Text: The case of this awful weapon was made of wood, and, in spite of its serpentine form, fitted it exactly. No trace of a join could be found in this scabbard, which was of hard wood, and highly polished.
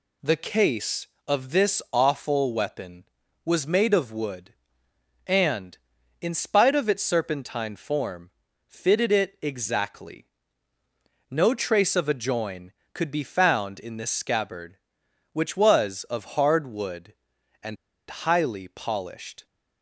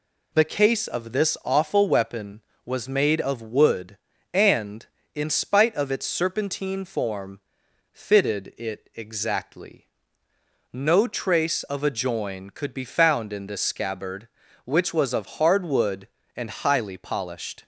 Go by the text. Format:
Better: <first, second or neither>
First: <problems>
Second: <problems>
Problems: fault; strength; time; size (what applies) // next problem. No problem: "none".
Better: second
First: pauses between "and" and "highly"; slight; at 17.7 s; 0.33 s long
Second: none